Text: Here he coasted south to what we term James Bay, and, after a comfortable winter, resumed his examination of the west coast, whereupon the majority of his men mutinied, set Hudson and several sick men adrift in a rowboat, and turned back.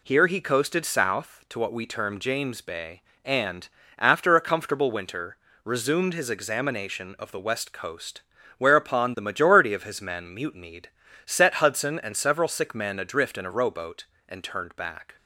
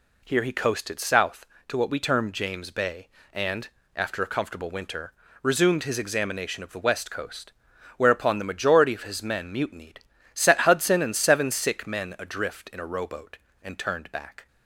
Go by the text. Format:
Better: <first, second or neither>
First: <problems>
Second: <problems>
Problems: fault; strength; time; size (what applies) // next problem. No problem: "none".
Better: first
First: none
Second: says "seven" for "several"; at 11.1 s